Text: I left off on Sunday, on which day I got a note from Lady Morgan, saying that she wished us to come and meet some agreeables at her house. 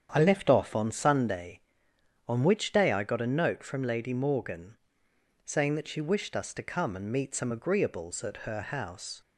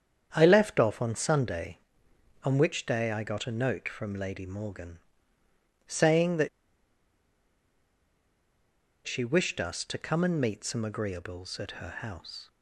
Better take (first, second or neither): first